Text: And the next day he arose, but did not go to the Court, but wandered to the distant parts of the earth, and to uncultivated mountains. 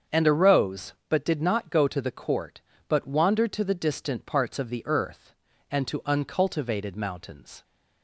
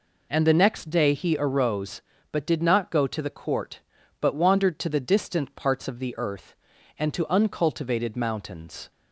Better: second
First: starts louder than the rest; until 1.2 s; 7 dB // skips "the next day he"; at 0.2 s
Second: none

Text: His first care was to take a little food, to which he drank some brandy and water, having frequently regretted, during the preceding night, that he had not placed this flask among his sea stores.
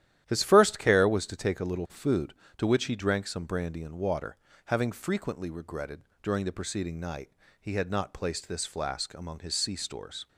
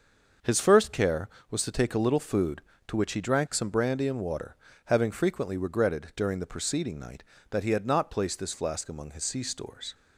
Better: second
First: starts louder than the rest; strong; until 1.2 s; 11.5 dB // skips "that"; at 7.4 s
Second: starts louder than the rest; until 1.6 s; 6.5 dB

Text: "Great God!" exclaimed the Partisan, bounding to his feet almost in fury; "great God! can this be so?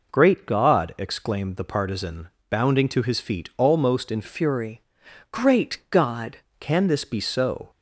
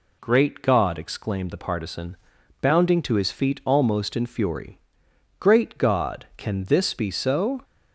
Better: second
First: changes voice from "fury" to "God"; from 4.2 to 6.3 s; 2.1 s long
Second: none

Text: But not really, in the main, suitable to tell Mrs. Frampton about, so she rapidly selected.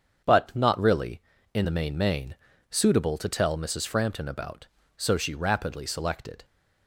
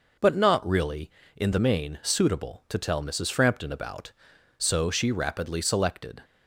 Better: second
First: starts louder than the rest; until 1.5 s; 7 dB // says "main" twice; at 1.9 s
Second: none

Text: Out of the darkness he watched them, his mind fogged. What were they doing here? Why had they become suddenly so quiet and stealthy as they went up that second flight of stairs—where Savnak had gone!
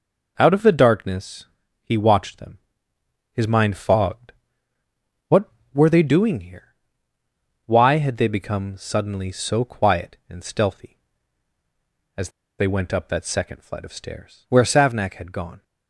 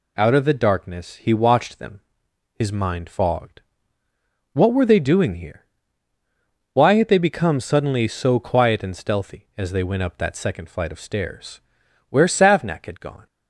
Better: second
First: pauses between "darkness" and "he"; slight; at 1.4 s; 0.36 s long // pauses between "as" and "they"; slight; at 12.2 s; 0.29 s long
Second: none

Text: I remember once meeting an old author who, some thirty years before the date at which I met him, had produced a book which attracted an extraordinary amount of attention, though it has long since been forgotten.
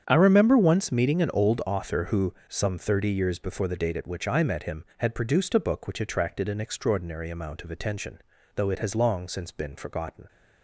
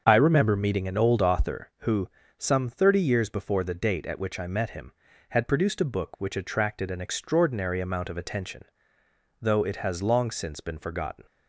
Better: first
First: starts louder than the rest; strong; until 1.0 s; 8 dB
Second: starts louder than the rest; until 1.0 s; 7 dB // skips "once"; at 0.5 s

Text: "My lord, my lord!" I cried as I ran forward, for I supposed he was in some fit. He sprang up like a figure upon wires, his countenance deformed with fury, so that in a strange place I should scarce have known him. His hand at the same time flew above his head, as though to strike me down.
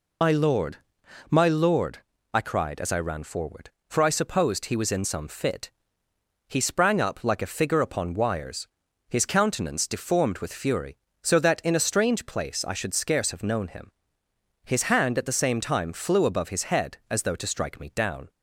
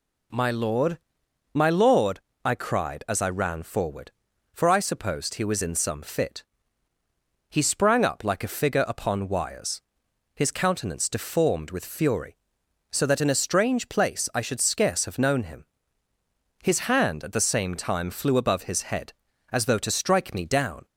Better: second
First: loses the start of "My"; at 0.2 s; 60 ms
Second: none

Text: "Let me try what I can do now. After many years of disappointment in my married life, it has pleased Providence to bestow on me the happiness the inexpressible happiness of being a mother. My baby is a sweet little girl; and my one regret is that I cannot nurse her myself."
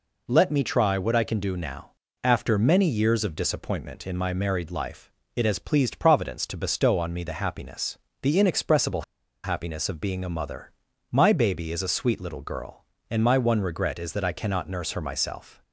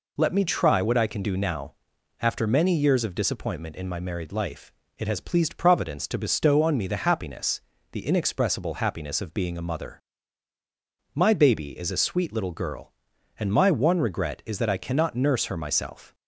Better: second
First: pauses between "happiness" and "the"; slight; at 7.9 s; 0.24 s long // pauses between "inexpressible" and "happiness"; at 9.0 s; 0.41 s long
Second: pauses between "happiness" and "the"; slight; at 7.6 s; 0.30 s long

